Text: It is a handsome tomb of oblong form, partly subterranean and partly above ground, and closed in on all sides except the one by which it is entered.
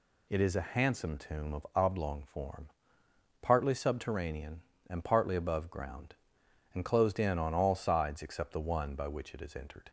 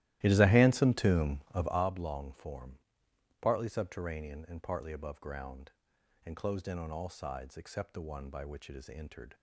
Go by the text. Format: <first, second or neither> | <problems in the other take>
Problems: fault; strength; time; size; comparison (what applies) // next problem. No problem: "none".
first | starts louder than the rest; strong; until 1.8 s; 14.5 dB